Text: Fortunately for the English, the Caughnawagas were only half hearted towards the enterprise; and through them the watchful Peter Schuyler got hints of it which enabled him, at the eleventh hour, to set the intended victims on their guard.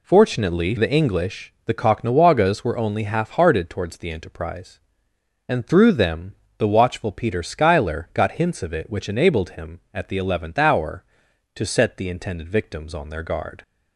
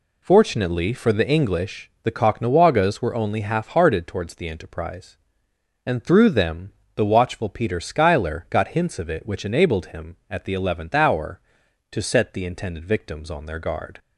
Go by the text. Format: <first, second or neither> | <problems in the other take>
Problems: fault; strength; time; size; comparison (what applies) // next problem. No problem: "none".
second | skips "for"; at 0.7 s // pauses between "them" and "the"; slight; at 6.3 s; 0.24 s long; slight in the second